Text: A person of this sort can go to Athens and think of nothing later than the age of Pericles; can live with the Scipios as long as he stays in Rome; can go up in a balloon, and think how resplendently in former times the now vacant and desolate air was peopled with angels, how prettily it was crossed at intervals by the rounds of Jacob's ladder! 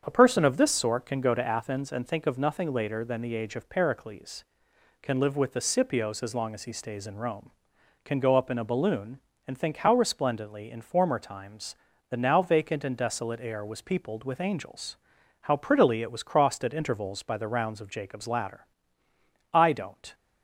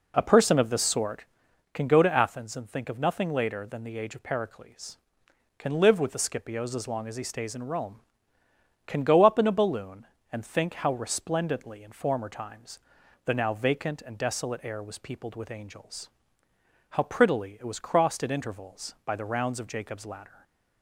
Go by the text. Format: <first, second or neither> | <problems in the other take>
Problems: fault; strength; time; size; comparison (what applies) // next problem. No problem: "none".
second | starts louder than the rest; strong; until 1.0 s; 7.5 dB // pauses between "times" and "the"; slight; at 11.7 s; 0.36 s long; noticeable in the second // goes on to say "I don't"; from 19.5 s on; 0.60 s long